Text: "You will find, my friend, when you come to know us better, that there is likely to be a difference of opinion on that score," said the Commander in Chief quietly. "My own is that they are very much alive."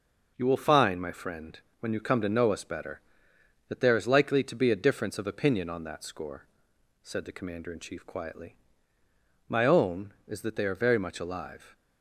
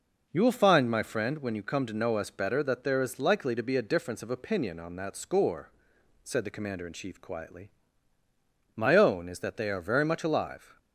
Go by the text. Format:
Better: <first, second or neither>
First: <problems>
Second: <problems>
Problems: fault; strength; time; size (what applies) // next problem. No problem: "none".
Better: neither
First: none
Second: none